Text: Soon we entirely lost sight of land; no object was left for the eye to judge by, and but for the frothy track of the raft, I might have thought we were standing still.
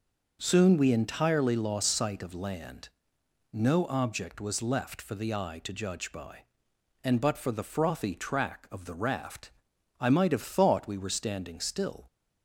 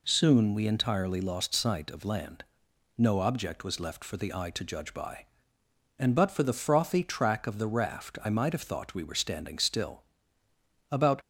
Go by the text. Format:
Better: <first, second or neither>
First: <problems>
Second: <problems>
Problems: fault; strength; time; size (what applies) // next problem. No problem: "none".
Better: first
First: none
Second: goes on to say "About"; slight; from 10.9 s on; 0.30 s long